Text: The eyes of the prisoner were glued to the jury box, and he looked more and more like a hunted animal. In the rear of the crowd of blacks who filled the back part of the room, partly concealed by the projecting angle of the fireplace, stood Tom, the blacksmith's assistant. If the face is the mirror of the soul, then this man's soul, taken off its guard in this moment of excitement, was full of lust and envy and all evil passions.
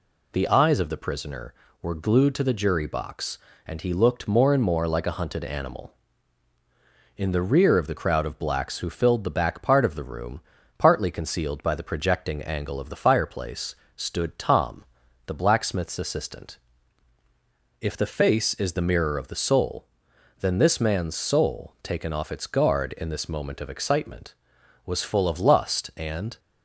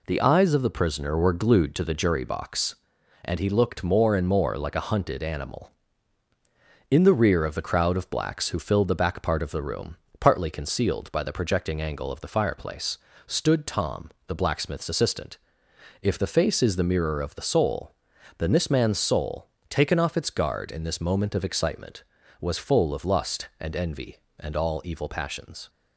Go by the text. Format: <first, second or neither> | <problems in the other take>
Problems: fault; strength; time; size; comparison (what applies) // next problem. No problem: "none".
second | stops before "envy and all evil passions"; at 26.3 s